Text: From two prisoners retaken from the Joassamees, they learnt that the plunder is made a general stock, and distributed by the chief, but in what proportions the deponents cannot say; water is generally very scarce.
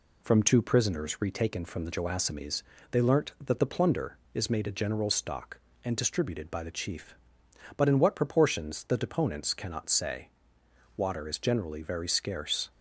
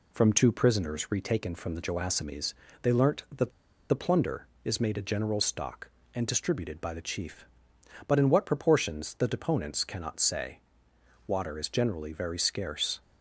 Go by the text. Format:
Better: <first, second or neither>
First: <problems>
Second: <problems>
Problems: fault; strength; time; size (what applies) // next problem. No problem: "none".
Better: first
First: none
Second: pauses between "that" and "the"; at 3.5 s; 0.39 s long